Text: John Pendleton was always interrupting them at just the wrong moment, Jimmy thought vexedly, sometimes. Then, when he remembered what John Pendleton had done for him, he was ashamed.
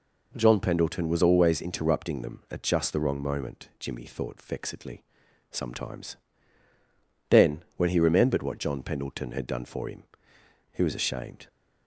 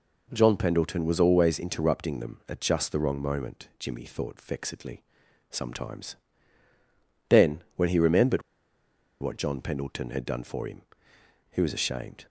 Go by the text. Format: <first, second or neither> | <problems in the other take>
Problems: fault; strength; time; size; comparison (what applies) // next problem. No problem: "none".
first | pauses between "remembered" and "what"; noticeable; at 8.4 s; 0.80 s long